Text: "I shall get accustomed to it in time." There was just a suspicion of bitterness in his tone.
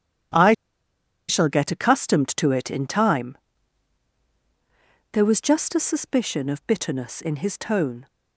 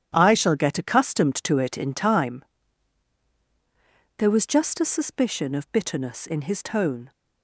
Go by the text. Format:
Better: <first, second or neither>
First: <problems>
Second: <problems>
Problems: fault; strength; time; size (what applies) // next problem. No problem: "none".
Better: second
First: starts louder than the rest; strong; until 2.0 s; 10 dB // pauses between "I" and "shall"; noticeable; at 0.5 s; 0.73 s long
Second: starts louder than the rest; strong; until 1.1 s; 10 dB